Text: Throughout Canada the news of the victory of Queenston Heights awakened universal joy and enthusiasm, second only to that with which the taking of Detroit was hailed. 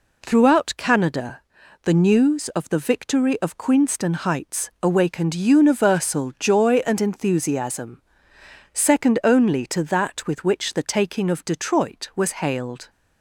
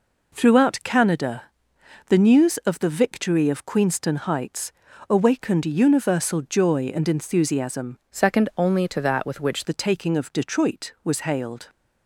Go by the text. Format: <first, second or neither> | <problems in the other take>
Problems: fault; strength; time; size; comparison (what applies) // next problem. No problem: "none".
first | pauses between "Canada" and "the"; noticeable; at 1.4 s; 0.64 s long; also in the first // pauses between "Heights" and "awakened"; at 4.7 s; 0.38 s long // changes voice from "second" to "which"; from 8.1 to 9.6 s; 1.5 s long